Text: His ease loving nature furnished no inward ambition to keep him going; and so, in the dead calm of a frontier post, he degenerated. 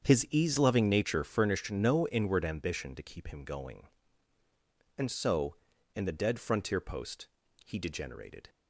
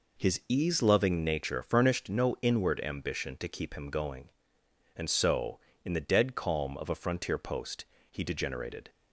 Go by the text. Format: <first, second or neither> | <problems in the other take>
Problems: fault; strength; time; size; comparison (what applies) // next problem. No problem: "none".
second | starts louder than the rest; strong; until 1.0 s; 7.5 dB // skips "calm of a"; at 6.4 s